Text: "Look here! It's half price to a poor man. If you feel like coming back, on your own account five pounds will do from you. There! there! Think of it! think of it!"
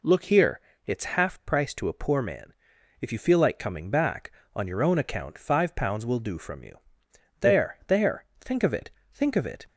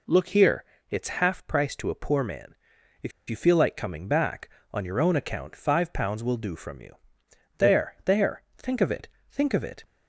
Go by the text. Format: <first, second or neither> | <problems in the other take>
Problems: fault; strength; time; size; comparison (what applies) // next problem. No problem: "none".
first | pauses between "If" and "you"; slight; at 3.1 s; 0.19 s long